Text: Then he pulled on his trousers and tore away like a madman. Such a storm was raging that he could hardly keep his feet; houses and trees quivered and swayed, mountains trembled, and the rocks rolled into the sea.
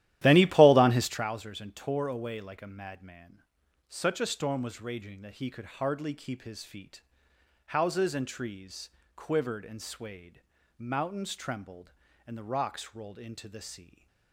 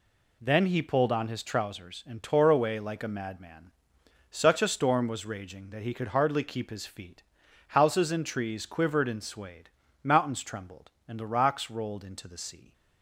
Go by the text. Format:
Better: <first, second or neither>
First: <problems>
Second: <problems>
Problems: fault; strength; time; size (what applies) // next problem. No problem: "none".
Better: second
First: starts louder than the rest; strong; until 1.3 s; 13.5 dB // pauses between "trees" and "quivered"; slight; at 8.8 s; 0.28 s long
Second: none